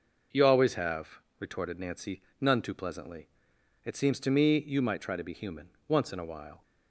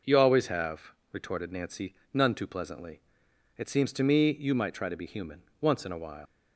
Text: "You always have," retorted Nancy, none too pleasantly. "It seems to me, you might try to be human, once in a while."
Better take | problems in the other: first | leaves "while" unfinished; at 6.2 s; 95 ms

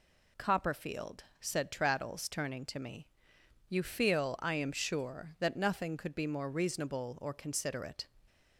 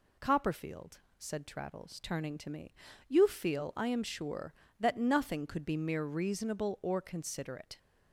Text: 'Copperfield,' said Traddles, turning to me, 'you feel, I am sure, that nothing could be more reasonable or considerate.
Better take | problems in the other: first | says "mere" for "more"; at 5.7 s

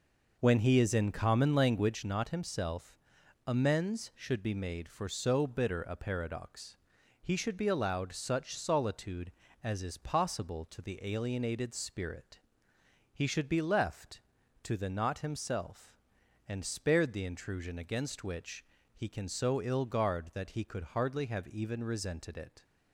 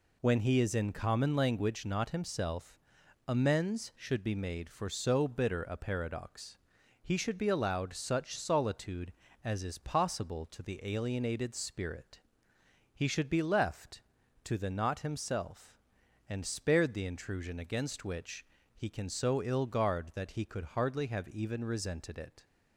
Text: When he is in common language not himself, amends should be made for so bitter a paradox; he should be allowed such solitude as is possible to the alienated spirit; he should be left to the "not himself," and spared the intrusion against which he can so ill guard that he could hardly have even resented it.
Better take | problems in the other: second | starts louder than the rest; noticeable; until 2.2 s; 5.5 dB // pauses between "which" and "he"; slight; at 18.6 s; 0.32 s long; slight in the second

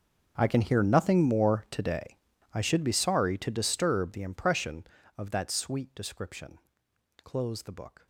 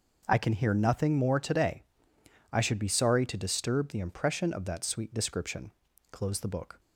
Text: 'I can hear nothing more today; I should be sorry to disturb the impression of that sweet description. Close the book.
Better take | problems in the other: second | gets quieter; strong; throughout; 20.5 dB

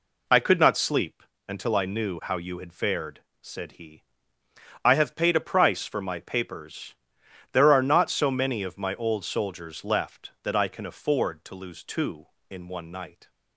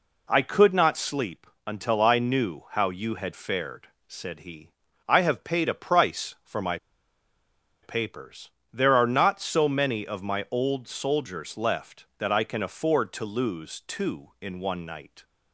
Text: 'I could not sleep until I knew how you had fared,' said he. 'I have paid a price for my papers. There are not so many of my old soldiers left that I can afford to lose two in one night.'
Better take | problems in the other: first | pauses between "sleep" and "until"; slight; at 1.4 s; 0.20 s long; slight in the first // pauses between "my" and "papers"; at 6.7 s; 1.0 s long

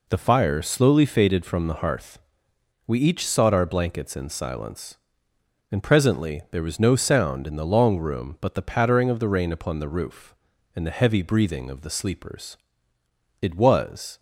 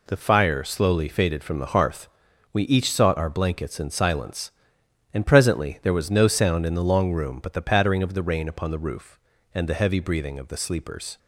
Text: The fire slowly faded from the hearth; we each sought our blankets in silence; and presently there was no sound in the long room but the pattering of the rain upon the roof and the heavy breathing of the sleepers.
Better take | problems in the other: second | goes on to say "It was"; noticeable; from 13.4 s on; 0.78 s long

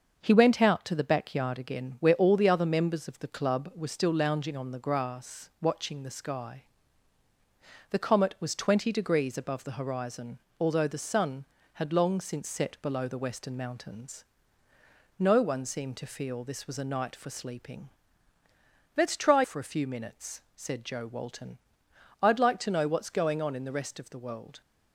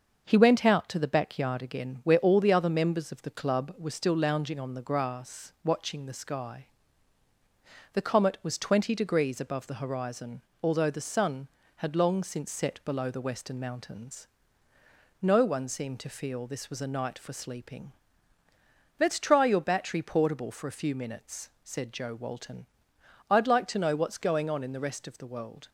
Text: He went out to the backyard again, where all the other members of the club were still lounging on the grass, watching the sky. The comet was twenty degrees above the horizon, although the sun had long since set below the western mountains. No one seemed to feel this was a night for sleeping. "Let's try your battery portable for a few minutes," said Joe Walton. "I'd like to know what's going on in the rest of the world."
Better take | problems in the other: second | starts louder than the rest; until 1.2 s; 6.5 dB; also in the second // skips "your battery portable"; at 19.4 s

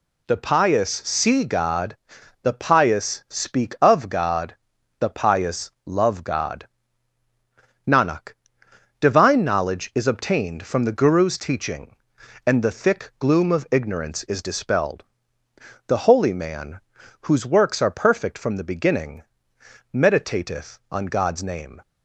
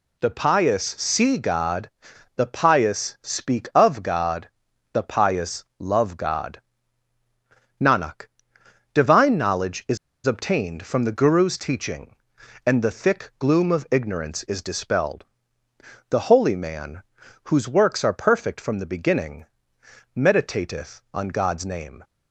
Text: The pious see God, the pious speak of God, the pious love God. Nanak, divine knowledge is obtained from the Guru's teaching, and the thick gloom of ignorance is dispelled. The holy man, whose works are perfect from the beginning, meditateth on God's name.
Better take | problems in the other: first | pauses between "is" and "obtained"; slight; at 9.9 s; 0.28 s long

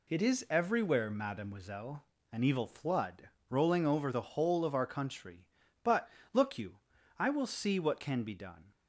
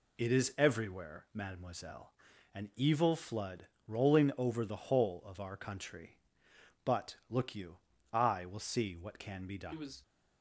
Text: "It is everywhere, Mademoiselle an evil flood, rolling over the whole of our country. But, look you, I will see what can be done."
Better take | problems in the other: first | pauses between "Mademoiselle" and "an"; at 2.1 s; 0.40 s long; slight in the first // goes on to say "He was"; slight; from 9.7 s on; 0.30 s long

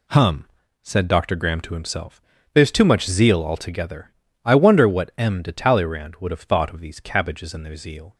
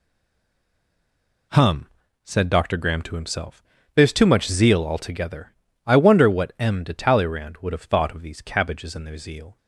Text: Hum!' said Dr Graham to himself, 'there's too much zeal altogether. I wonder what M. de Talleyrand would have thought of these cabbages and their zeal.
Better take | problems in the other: first | stays silent before the first word; noticeable; until 1.5 s; 1.5 s long

